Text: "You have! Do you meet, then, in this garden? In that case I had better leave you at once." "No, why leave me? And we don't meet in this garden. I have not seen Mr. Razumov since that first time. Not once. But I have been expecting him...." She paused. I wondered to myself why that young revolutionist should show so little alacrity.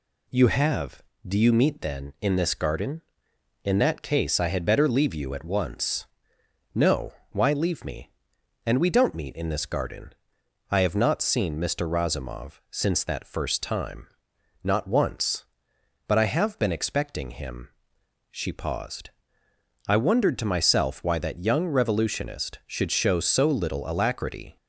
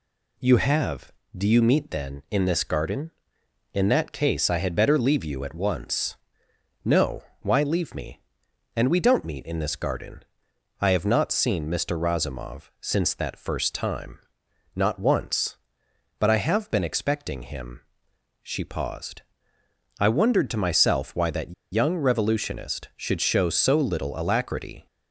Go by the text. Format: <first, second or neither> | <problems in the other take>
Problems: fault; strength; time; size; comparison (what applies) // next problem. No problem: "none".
first | pauses between "that" and "young"; slight; at 21.5 s; 0.19 s long